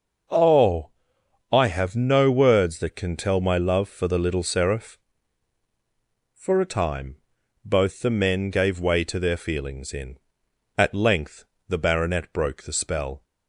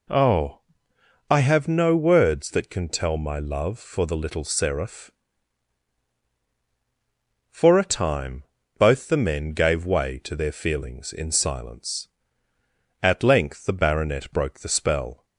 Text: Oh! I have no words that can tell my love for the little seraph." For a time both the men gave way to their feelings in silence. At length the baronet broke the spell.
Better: second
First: starts louder than the rest; noticeable; until 1.9 s; 6 dB // pauses between "time" and "both"; noticeable; at 7.1 s; 0.48 s long // skips "silence"; at 10.4 s // pauses between "length" and "the"; slight; at 11.4 s; 0.24 s long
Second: pauses between "time" and "both"; slight; at 8.4 s; 0.34 s long

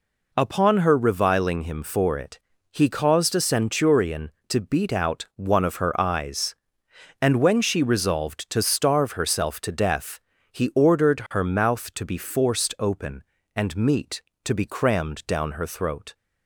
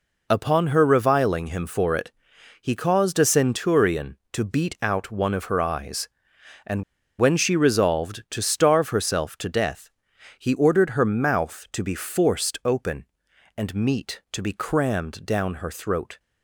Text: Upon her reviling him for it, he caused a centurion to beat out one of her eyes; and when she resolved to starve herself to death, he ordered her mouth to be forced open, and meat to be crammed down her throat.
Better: first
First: none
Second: pauses between "and" and "when"; at 6.8 s; 0.37 s long

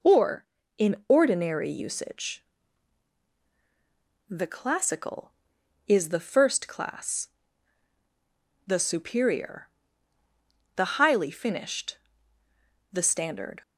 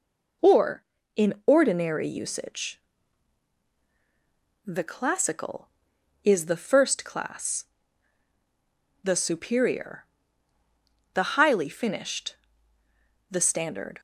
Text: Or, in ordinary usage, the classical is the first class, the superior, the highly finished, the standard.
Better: neither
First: none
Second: none

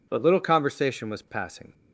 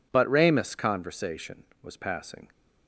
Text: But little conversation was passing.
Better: first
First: none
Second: says "ramus" for "little"; at 0.2 s

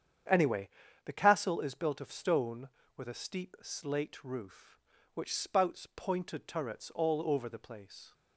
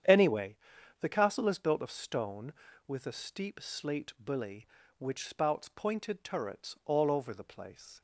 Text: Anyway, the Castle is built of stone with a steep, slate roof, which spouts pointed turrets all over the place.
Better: first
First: starts louder than the rest; strong; until 1.6 s; 8.5 dB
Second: starts louder than the rest; strong; until 1.5 s; 9 dB // says "bully" for "roof"; at 4.2 s

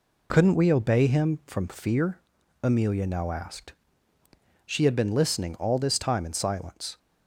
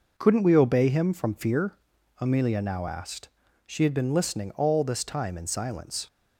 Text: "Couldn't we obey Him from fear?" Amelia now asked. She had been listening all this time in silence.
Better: neither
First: none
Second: none

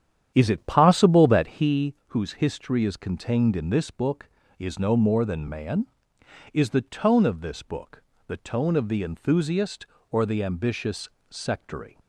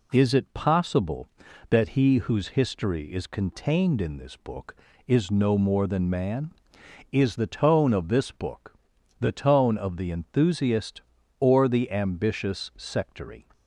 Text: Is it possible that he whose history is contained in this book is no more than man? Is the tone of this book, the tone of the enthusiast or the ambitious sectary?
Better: second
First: starts louder than the rest; strong; until 1.7 s; 9.5 dB // pauses between "ambitious" and "sectary"; slight; at 11.0 s; 0.24 s long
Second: none

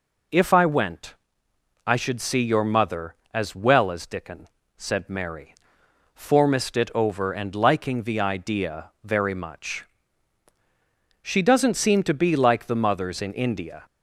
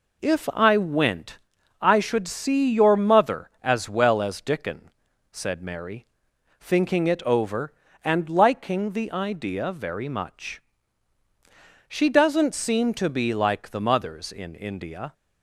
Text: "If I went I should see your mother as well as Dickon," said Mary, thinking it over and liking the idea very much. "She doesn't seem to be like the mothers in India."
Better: second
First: pauses between "went" and "I"; noticeable; at 1.1 s; 0.72 s long // says "formist" for "thinking"; at 6.1 s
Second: pauses between "went" and "I"; at 1.3 s; 0.44 s long

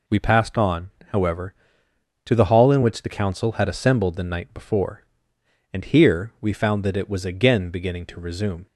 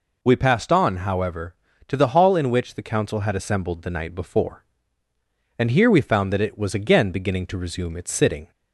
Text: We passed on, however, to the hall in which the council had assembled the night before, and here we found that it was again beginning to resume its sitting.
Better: second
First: stops before "its sitting"; at 8.6 s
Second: none

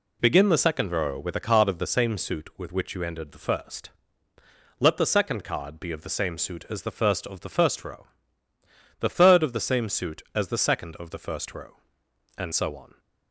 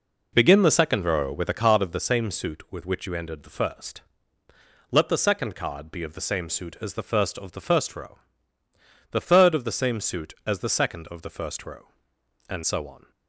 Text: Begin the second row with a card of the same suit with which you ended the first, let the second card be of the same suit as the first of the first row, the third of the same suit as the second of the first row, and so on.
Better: first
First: none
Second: starts louder than the rest; noticeable; until 1.8 s; 4.5 dB

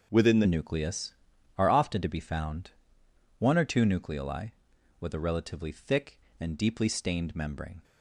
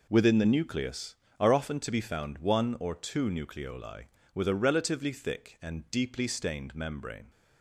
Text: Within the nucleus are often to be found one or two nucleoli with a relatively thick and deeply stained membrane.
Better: second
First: changes voice at "nucleus"; from 0.4 s on; 7.4 s long // pauses between "found" and "one"; noticeable; at 2.7 s; 0.68 s long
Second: none

